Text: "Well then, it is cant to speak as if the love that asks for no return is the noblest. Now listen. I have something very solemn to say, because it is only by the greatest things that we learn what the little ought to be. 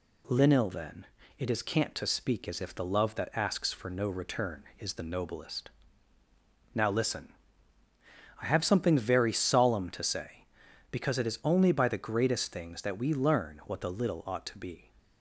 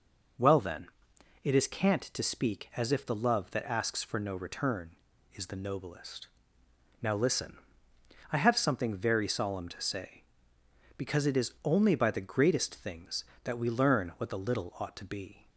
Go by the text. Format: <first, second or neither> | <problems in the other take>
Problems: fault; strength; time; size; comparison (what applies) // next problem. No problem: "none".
second | says "Linil" for "Well"; at 0.2 s